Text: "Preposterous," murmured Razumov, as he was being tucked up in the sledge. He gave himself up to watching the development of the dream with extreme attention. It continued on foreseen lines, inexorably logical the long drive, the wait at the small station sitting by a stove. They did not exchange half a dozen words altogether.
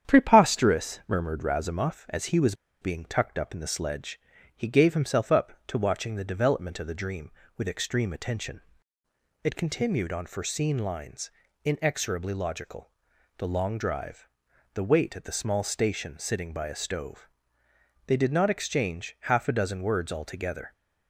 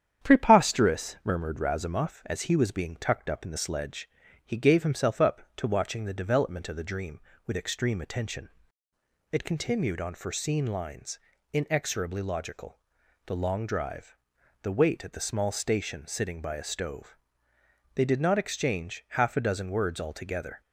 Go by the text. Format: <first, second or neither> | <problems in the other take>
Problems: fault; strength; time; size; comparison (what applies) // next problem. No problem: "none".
second | starts louder than the rest; strong; until 1.1 s; 9 dB; strong in the second // pauses between "was" and "being"; slight; at 2.5 s; 0.28 s long // pauses between "logical" and "the"; noticeable; at 12.9 s; 0.48 s long; noticeable in the second